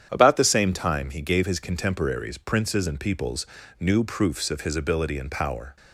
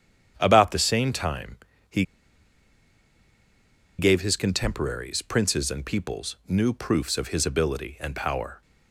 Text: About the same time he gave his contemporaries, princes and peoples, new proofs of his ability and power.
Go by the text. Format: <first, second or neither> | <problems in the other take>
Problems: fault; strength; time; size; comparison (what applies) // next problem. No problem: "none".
first | starts louder than the rest; strong; until 1.3 s; 9 dB; strong in the first // pauses between "time" and "he"; slight; at 1.5 s; 0.34 s long // pauses between "he" and "gave"; strong; at 2.0 s; 1.9 s long